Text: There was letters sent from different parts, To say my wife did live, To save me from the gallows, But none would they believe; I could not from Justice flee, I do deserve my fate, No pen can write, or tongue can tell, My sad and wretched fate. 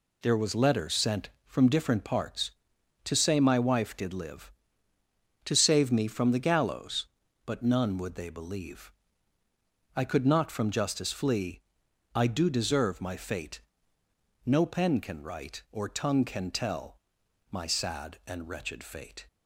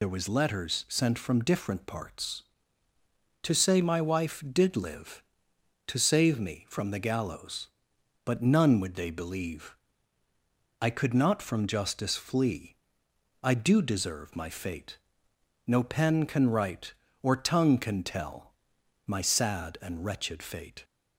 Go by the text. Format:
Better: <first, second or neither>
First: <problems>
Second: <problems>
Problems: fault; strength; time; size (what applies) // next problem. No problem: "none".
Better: first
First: none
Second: loses the start of "There"; at 0.0 s; 65 ms